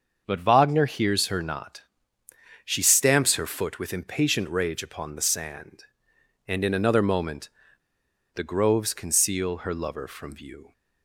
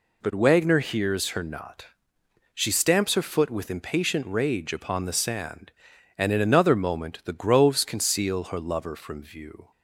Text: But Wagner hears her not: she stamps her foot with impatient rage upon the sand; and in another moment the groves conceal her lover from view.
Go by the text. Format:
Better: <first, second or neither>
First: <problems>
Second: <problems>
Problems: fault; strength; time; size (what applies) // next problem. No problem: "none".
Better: second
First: starts louder than the rest; until 1.2 s; 6.5 dB // pauses between "moment" and "the"; noticeable; at 7.5 s; 0.83 s long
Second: none